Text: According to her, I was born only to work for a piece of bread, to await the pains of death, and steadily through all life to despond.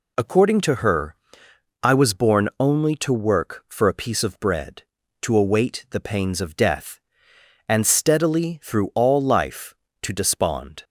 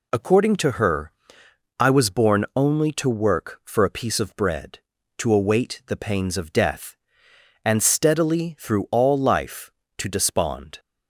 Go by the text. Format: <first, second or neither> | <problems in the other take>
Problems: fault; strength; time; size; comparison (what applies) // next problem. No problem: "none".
neither | none